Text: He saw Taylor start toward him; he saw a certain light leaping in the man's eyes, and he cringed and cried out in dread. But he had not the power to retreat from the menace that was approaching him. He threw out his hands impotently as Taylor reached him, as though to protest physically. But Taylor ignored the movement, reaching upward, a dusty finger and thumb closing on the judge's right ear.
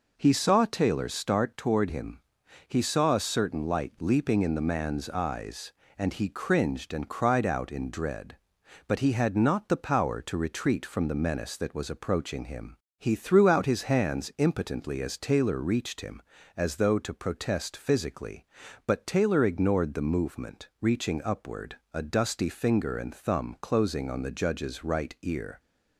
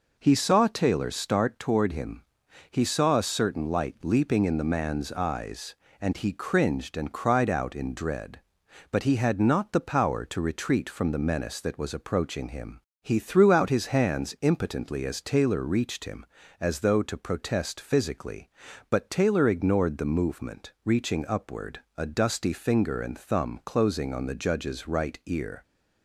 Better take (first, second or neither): neither